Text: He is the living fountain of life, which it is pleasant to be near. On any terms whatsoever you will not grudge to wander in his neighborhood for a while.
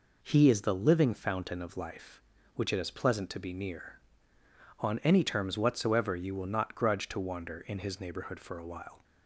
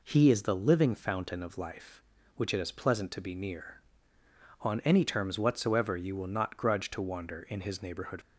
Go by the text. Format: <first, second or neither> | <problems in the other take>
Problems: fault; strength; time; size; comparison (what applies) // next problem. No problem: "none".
first | stops before "for a while"; at 8.2 s